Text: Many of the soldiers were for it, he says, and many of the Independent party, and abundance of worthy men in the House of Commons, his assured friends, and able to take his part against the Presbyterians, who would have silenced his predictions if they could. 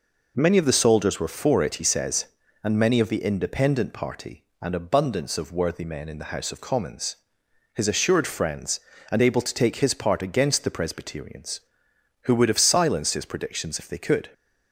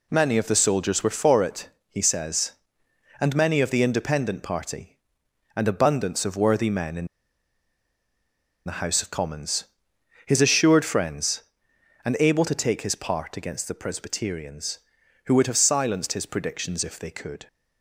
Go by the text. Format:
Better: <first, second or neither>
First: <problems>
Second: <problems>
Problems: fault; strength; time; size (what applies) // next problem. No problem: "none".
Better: first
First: none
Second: pauses between "in" and "the"; strong; at 7.0 s; 1.5 s long